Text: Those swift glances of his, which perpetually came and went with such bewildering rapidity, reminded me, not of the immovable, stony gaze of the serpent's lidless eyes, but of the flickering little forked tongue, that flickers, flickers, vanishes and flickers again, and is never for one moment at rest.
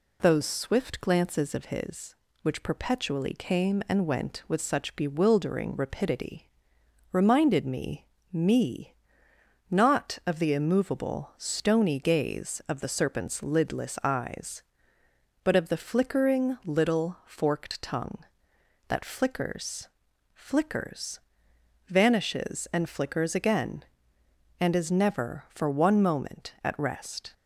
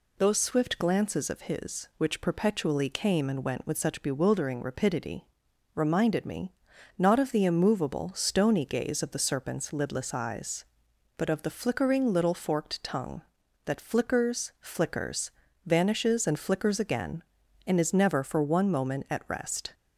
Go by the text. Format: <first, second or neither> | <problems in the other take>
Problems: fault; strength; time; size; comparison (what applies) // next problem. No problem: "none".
second | says "me" twice; at 8.3 s